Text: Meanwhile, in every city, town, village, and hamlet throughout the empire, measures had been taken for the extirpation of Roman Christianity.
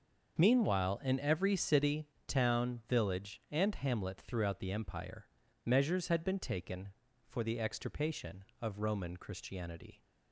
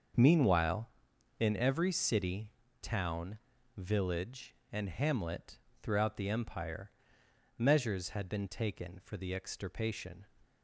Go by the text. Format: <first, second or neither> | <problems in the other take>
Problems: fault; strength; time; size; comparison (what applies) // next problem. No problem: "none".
first | starts louder than the rest; until 1.6 s; 6.5 dB; noticeable in the first // pauses between "hamlet" and "throughout"; slight; at 5.5 s; 0.24 s long // stops before "of Roman Christianity"; at 10.4 s